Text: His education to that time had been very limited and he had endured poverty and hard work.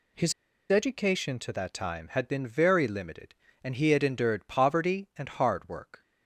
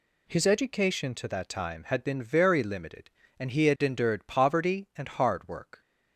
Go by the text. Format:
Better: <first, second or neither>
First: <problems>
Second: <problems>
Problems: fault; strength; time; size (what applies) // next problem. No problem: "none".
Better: second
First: pauses between "His" and "education"; at 0.3 s; 0.38 s long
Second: none